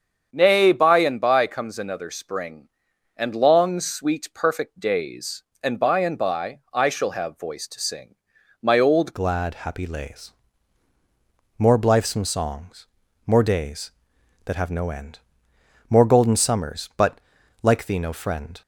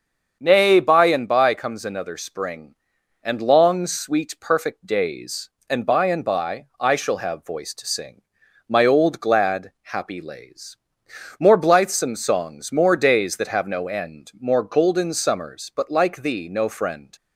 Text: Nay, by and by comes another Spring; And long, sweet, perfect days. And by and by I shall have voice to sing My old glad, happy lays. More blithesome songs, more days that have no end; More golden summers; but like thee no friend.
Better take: second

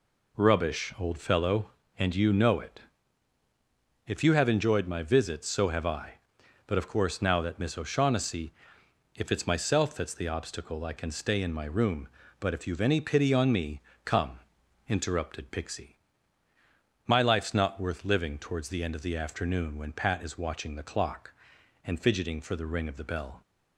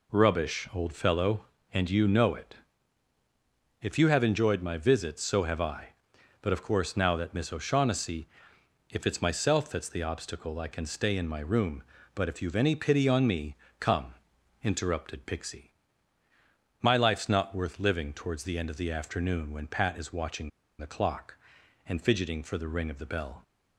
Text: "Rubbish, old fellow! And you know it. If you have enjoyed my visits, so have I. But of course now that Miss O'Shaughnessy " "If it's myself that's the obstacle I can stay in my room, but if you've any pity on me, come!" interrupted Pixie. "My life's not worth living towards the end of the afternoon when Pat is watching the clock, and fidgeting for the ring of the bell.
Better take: first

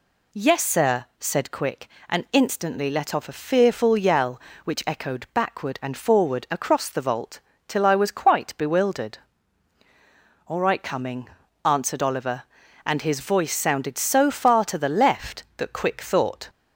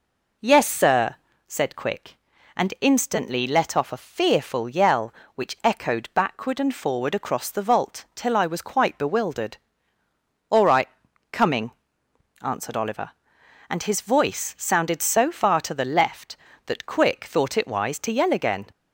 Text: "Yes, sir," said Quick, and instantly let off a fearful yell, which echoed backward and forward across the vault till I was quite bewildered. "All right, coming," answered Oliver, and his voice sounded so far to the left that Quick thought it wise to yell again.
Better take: second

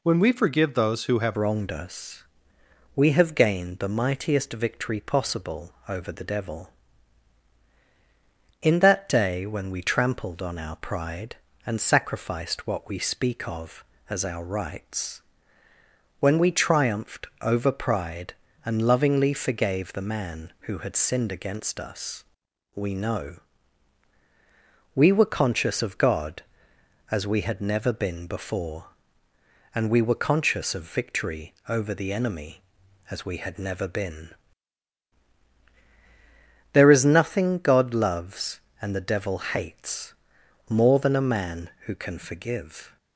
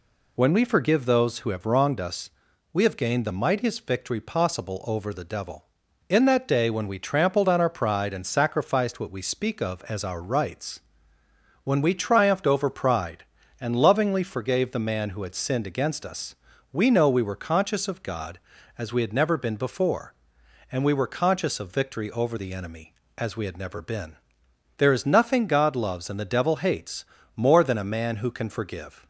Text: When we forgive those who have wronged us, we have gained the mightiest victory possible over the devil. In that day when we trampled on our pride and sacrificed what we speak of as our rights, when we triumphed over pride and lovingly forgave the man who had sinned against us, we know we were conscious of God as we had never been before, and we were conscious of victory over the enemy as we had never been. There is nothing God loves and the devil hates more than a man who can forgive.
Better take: second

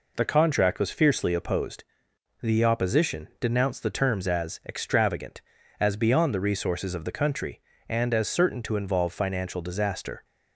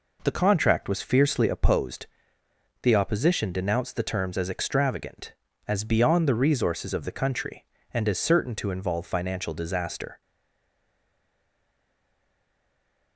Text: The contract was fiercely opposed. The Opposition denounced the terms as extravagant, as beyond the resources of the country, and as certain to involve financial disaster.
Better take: first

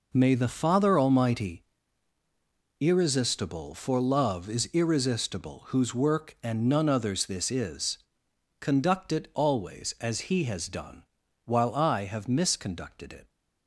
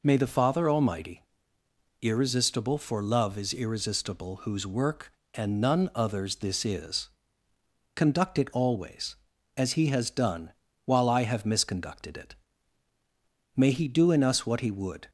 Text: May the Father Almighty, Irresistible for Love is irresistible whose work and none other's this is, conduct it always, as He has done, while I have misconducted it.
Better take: first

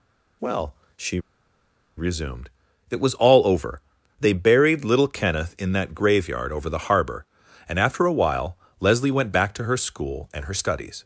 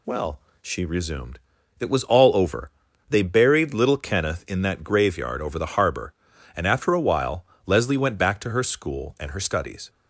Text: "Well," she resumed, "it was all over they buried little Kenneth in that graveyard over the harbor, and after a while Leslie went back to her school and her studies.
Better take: second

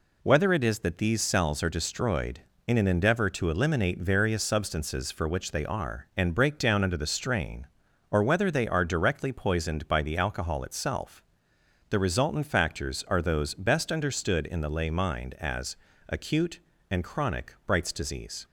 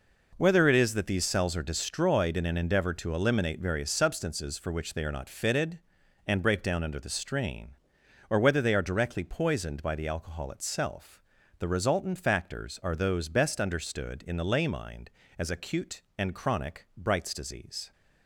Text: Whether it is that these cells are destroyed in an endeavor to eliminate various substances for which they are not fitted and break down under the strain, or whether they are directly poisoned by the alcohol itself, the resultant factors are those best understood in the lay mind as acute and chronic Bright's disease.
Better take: second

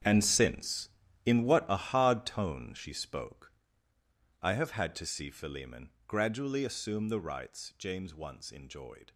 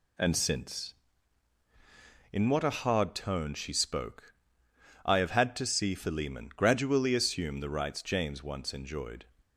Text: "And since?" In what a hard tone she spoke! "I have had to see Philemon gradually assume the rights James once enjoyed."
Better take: second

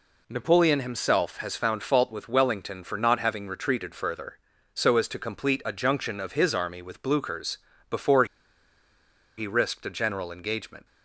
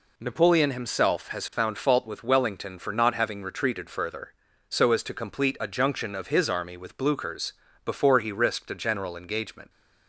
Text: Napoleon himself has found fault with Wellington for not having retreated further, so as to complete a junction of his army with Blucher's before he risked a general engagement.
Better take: second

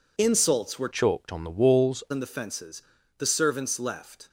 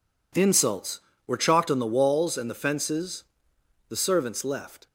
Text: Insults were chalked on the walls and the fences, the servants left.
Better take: second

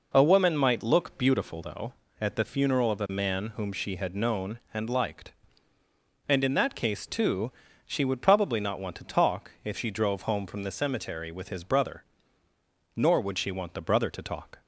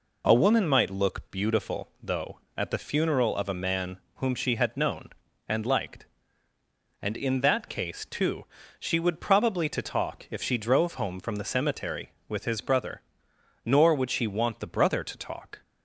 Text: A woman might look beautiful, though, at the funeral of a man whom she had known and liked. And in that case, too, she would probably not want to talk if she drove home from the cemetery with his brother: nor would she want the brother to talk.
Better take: first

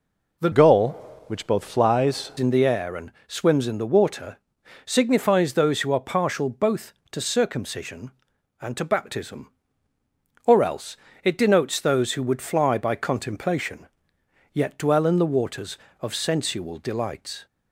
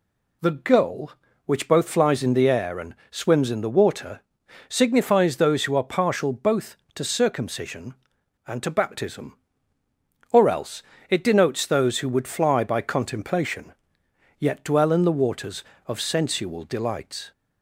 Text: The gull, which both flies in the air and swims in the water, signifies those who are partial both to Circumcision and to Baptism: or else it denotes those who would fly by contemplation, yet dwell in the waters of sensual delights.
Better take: second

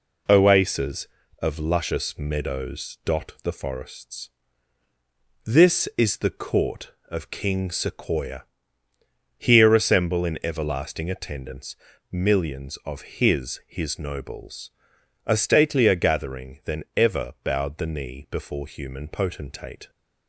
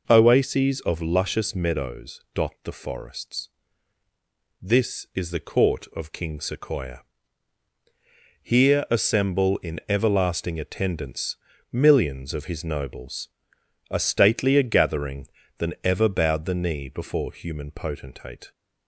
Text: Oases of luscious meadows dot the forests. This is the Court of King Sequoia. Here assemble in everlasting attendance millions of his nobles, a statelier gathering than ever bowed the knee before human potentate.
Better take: second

